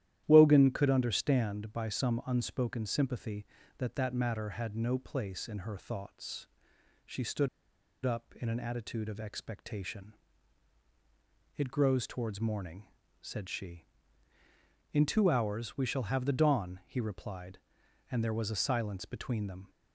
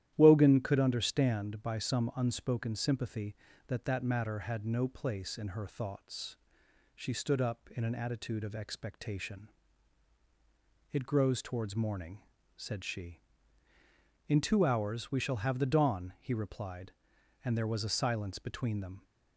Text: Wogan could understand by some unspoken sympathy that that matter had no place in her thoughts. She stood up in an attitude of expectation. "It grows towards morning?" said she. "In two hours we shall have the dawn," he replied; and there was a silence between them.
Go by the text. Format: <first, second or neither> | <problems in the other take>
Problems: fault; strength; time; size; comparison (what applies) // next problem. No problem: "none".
second | starts louder than the rest; strong; until 1.2 s; 12 dB; strong in the second // pauses between "stood" and "up"; noticeable; at 7.4 s; 0.57 s long